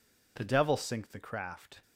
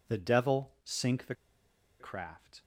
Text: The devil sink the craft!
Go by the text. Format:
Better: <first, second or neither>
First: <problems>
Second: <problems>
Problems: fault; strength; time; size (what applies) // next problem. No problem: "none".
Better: first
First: none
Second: pauses between "the" and "craft"; noticeable; at 1.3 s; 0.66 s long